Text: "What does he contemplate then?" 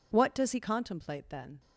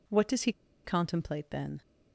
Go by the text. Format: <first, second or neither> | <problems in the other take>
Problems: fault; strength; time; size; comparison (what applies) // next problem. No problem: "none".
first | pauses between "he" and "contemplate"; slight; at 0.5 s; 0.32 s long